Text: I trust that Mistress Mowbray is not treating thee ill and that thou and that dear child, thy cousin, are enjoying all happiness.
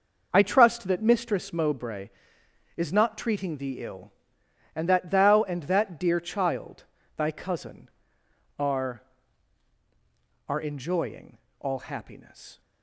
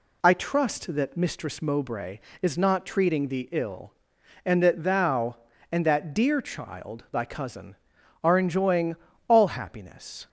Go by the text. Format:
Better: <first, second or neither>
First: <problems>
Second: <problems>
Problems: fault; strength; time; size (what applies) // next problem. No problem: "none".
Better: second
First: says "are" twice; at 10.4 s // pauses between "enjoying" and "all"; slight; at 11.3 s; 0.22 s long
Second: pauses between "enjoying" and "all"; slight; at 8.9 s; 0.32 s long